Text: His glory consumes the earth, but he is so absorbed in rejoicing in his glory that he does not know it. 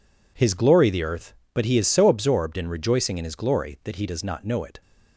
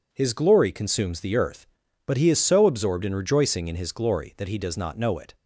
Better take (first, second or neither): second